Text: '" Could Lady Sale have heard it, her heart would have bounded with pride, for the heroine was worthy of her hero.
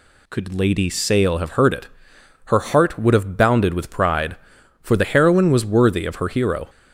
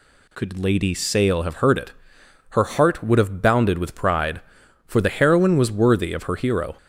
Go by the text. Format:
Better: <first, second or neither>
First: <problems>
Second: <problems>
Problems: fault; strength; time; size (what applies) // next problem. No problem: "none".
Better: neither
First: none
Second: none